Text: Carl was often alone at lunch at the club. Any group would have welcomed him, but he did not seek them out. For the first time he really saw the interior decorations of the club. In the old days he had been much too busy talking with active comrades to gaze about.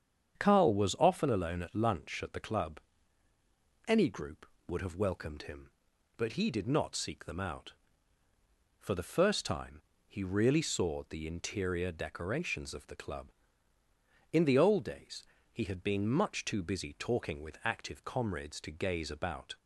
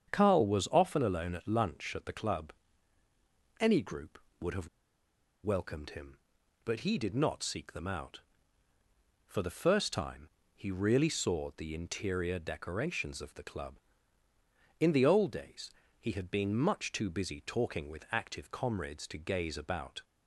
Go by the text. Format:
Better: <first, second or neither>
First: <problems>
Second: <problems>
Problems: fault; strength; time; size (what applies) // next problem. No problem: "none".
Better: first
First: starts louder than the rest; strong; until 1.4 s; 8 dB // pauses between "time" and "he"; slight; at 9.8 s; 0.28 s long // pauses between "days" and "he"; slight; at 15.2 s; 0.28 s long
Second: starts louder than the rest; strong; until 1.1 s; 8 dB // pauses between "have" and "welcomed"; noticeable; at 4.6 s; 0.75 s long // pauses between "time" and "he"; slight; at 10.2 s; 0.28 s long // pauses between "days" and "he"; slight; at 15.7 s; 0.28 s long